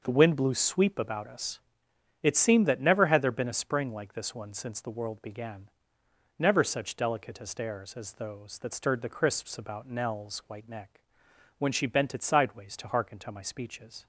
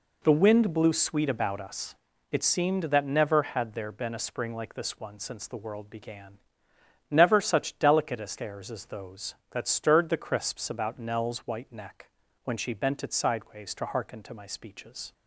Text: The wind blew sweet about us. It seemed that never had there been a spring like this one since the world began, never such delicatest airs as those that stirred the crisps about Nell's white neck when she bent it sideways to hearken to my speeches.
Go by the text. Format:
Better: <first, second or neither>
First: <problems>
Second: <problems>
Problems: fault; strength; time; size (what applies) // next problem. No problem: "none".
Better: second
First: says "sweep" for "sweet"; at 0.5 s // pauses between "neck" and "when"; noticeable; at 11.0 s; 0.56 s long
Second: pauses between "neck" and "when"; slight; at 12.0 s; 0.36 s long